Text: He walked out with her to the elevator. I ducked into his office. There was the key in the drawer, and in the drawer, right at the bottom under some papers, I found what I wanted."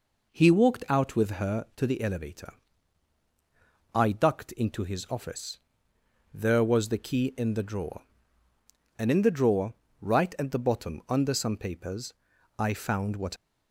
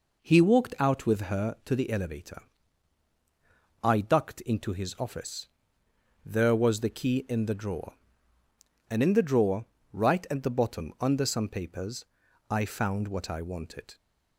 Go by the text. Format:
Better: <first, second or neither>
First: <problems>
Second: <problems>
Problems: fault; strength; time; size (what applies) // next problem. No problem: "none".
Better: second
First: stops before "I wanted"; at 13.3 s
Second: none